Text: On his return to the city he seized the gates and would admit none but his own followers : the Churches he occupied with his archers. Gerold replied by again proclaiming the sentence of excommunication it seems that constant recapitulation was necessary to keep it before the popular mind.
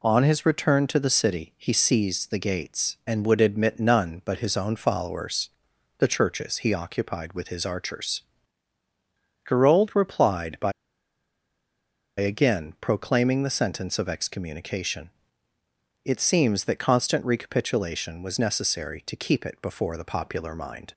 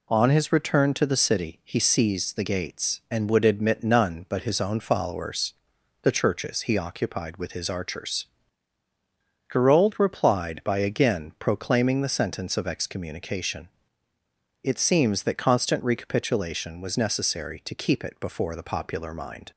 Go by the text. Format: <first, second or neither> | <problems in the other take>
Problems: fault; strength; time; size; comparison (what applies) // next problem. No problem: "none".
second | pauses between "by" and "again"; strong; at 10.7 s; 1.4 s long // pauses between "excommunication" and "it"; noticeable; at 15.0 s; 0.94 s long; noticeable in the second